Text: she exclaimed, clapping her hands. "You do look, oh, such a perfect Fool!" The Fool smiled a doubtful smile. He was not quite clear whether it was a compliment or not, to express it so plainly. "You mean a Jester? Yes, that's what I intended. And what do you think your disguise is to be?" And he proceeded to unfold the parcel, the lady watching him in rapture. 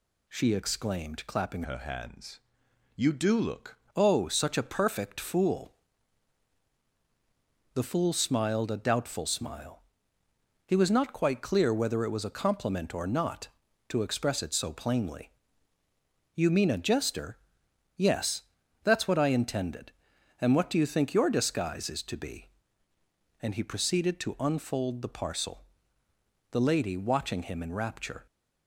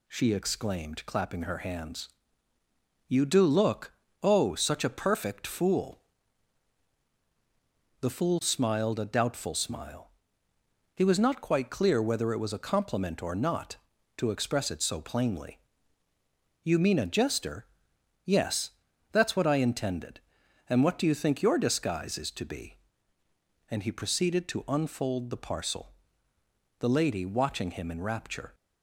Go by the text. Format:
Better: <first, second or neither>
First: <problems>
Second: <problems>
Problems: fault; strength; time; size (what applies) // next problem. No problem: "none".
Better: second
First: changes voice from "her" to "look"; from 1.6 to 3.7 s; 2.1 s long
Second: none